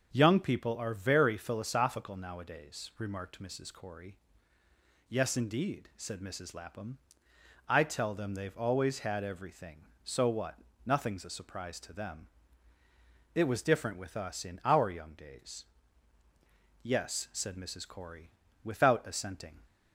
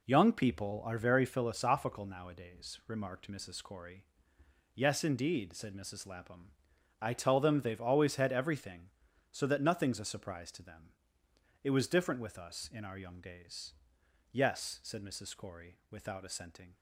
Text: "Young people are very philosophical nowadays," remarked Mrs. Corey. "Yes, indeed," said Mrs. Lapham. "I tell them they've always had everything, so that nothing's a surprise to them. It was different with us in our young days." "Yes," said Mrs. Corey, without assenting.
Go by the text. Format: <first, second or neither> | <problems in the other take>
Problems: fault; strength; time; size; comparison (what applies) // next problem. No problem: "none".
second | starts louder than the rest; until 1.1 s; 7 dB // says "what" for "that"; at 10.2 s